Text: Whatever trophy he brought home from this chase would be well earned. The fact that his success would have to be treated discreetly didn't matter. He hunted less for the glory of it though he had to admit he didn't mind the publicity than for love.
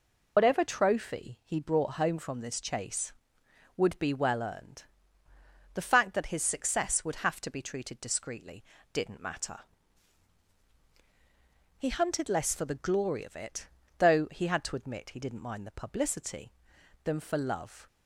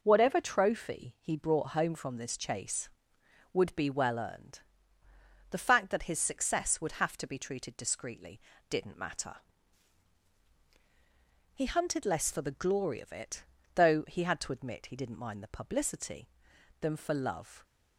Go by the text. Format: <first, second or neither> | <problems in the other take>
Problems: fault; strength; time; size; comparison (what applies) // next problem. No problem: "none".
second | loses the start of "Whatever"; at 0.3 s; 100 ms // pauses between "discreetly" and "didn't"; slight; at 8.6 s; 0.32 s long; slight in the second // pauses between "it" and "though"; slight; at 13.6 s; 0.32 s long; slight in the second